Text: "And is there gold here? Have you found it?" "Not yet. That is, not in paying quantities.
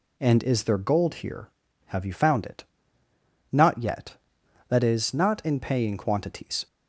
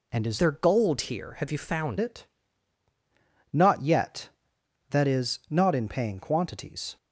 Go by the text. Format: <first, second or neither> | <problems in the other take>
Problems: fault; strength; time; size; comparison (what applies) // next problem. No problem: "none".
first | changes voice from "there" to "found"; from 0.3 to 1.9 s; 1.6 s long